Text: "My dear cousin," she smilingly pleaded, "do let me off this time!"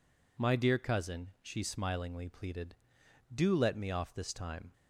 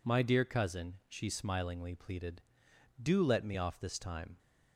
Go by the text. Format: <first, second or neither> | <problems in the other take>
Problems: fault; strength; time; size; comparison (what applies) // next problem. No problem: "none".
neither | none